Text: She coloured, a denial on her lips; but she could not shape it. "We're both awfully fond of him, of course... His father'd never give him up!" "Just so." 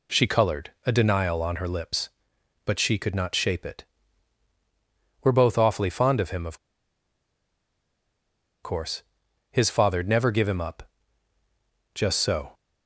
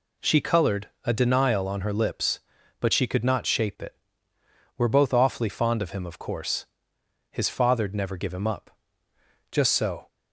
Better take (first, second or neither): second